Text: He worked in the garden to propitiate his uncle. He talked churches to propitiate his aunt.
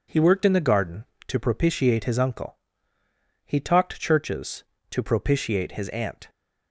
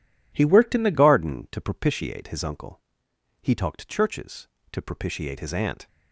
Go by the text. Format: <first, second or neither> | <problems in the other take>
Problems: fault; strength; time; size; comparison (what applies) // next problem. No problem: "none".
first | changes voice at "garden"; from 0.9 s on; 4.9 s long